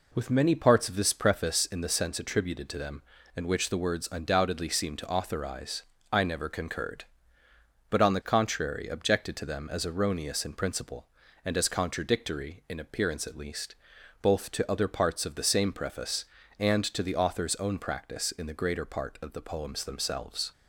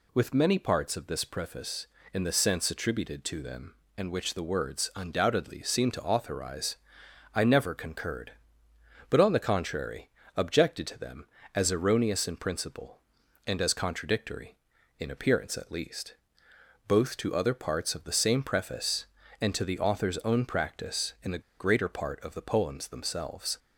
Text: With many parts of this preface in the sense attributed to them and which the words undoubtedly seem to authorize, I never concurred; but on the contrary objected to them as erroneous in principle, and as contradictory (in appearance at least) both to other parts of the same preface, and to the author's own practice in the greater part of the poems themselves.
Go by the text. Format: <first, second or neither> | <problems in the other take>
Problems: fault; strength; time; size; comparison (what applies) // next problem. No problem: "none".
first | pauses between "contrary" and "objected"; slight; at 10.0 s; 0.26 s long // pauses between "the" and "greater"; slight; at 21.4 s; 0.19 s long